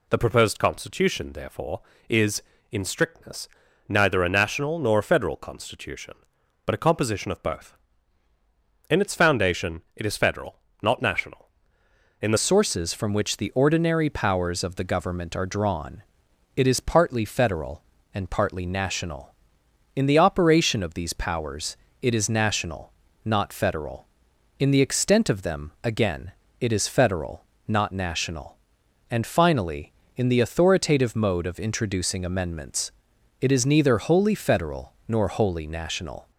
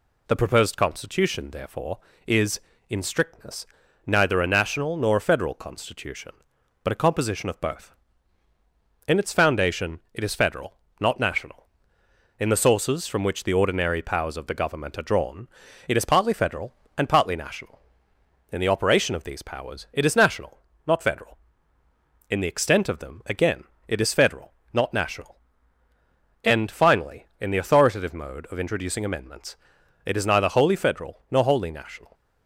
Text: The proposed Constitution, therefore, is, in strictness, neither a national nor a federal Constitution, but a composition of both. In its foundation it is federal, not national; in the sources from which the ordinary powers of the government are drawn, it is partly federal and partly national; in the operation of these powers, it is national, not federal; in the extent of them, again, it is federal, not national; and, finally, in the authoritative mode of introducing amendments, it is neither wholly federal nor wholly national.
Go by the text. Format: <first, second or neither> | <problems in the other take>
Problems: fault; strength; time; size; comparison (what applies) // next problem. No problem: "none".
second | changes voice at "sources"; from 12.3 s on; 24.0 s long